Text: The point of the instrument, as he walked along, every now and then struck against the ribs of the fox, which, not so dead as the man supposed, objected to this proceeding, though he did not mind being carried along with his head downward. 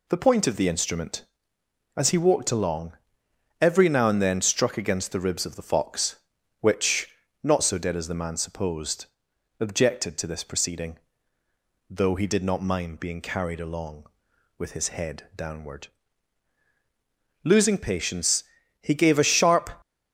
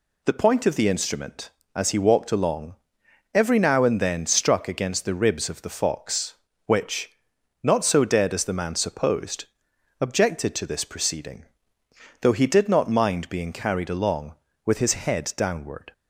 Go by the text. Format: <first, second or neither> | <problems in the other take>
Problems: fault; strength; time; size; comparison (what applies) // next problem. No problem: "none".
second | goes on to say "Losing patience he gave a sharp"; strong; from 17.4 s on; 2.2 s long